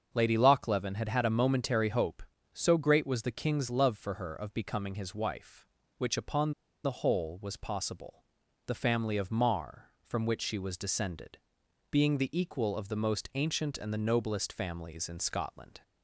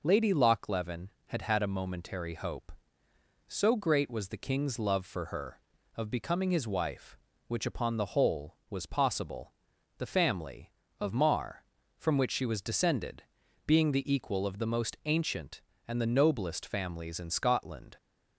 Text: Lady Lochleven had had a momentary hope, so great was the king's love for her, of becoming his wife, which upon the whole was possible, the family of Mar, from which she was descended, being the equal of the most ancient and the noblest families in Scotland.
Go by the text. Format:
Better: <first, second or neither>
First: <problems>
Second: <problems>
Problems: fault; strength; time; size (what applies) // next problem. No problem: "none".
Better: second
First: starts louder than the rest; until 1.1 s; 6.5 dB // pauses between "upon" and "the"; slight; at 6.5 s; 0.32 s long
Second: none